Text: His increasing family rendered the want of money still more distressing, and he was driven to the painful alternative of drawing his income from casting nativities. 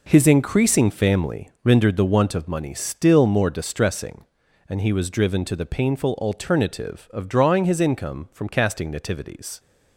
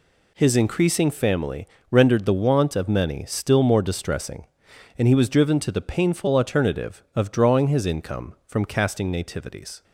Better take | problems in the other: first | pauses between "family" and "rendered"; slight; at 1.6 s; 0.24 s long; slight in the first // says "many" for "money"; at 2.8 s

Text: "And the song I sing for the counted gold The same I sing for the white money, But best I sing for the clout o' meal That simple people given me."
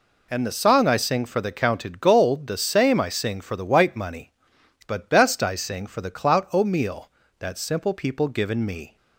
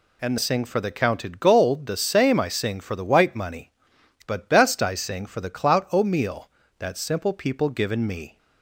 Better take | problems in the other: first | skips "the song I"; at 0.3 s

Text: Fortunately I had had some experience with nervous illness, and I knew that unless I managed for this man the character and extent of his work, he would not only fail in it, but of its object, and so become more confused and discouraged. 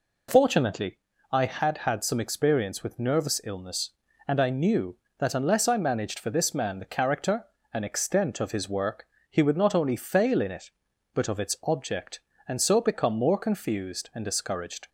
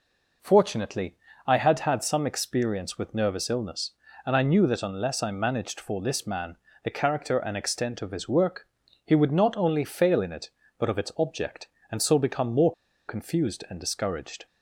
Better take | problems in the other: first | pauses between "Fortunately" and "I"; slight; at 1.1 s; 0.30 s long; slight in the first // pauses between "man" and "the"; slight; at 6.5 s; 0.26 s long // pauses between "more" and "confused"; slight; at 12.7 s; 0.36 s long

